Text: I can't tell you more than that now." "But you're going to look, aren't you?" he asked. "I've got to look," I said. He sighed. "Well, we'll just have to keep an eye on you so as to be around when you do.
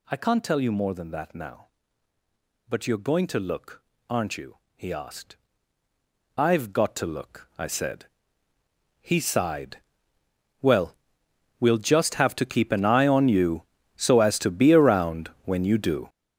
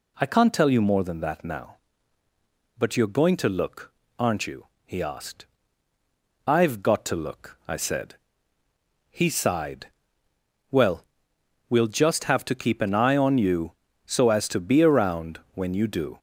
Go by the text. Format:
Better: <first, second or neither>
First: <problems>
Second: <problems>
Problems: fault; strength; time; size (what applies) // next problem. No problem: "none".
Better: second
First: gets louder; strong; throughout; 11 dB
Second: none